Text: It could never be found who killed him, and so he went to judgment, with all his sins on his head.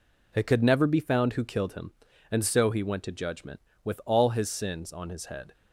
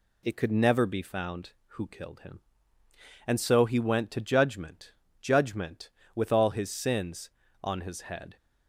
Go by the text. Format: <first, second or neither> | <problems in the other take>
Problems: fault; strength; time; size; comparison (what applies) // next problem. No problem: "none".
first | says "judgment" twice; at 5.1 s